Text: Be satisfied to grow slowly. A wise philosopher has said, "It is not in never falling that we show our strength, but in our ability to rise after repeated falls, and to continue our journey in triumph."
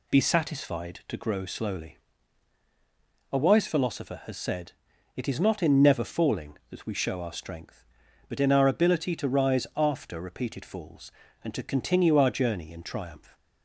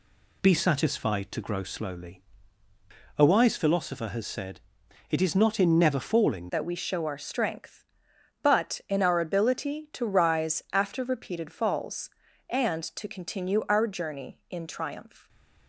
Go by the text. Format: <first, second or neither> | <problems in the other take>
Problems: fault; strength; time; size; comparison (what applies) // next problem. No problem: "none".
first | changes voice at "that"; from 6.4 s on; 8.8 s long // stays silent after the last word; slight; from 15.1 s on; 0.5 s long